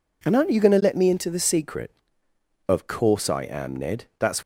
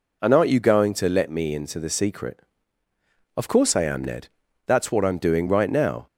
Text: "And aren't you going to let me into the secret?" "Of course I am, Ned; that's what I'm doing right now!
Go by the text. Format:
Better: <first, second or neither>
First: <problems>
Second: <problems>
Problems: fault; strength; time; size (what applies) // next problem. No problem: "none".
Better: second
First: stops before "what I'm doing right now"; at 4.4 s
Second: none